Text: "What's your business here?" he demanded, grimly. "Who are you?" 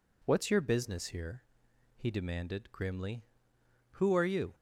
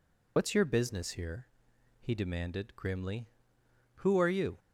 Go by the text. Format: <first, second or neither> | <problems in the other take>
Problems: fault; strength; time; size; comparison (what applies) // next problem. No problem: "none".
first | loses the start of "What's"; at 0.3 s; 105 ms